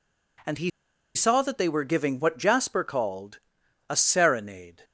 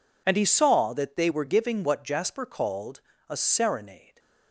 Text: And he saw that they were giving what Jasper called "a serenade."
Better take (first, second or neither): second